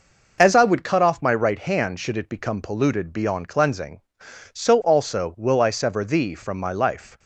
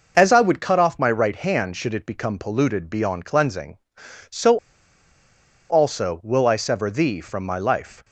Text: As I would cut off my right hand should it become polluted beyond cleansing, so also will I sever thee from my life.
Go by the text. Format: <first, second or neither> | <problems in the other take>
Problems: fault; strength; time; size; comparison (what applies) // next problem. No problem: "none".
first | pauses between "so" and "also"; at 4.5 s; 1.1 s long